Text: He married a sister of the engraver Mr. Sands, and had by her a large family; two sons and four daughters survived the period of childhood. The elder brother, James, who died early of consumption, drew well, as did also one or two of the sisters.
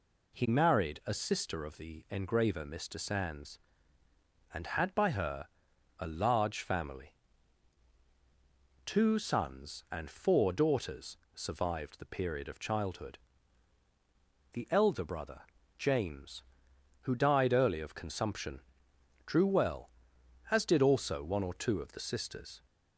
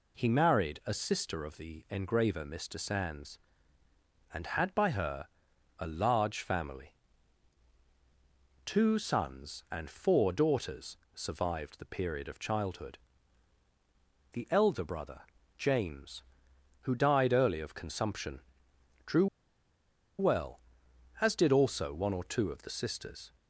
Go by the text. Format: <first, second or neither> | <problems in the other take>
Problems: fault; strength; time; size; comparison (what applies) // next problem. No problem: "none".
first | pauses between "her" and "a"; noticeable; at 5.2 s; 0.50 s long; noticeable in the first // pauses between "daughters" and "survived"; slight; at 10.9 s; 0.18 s long; slight in the first // pauses between "drew" and "well"; noticeable; at 19.2 s; 0.93 s long